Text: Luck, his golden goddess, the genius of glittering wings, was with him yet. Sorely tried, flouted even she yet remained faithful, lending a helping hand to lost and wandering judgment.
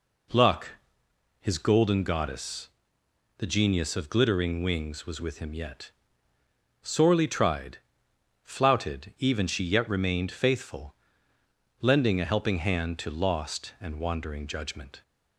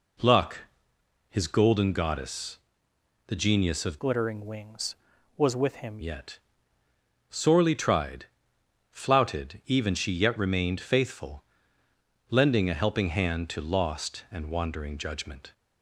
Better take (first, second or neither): first